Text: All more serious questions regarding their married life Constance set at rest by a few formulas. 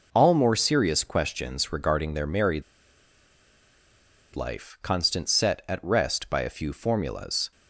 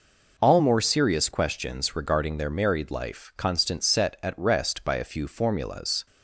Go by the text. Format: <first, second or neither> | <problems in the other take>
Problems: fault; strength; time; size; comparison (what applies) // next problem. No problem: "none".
second | pauses between "married" and "life"; strong; at 2.6 s; 1.7 s long